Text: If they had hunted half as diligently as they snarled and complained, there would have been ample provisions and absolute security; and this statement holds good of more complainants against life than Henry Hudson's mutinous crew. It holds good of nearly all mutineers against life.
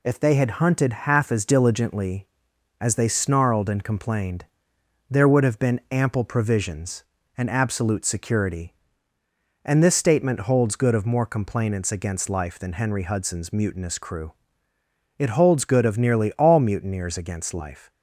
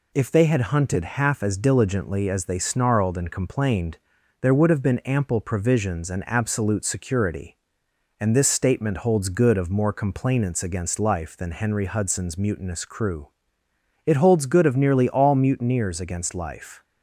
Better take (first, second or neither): neither